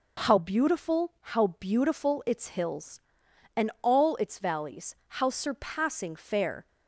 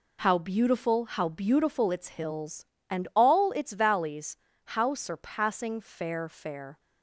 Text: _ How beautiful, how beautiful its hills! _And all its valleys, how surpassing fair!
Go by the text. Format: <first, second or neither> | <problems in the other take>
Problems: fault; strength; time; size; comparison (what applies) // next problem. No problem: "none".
first | says "fair" twice; at 6.2 s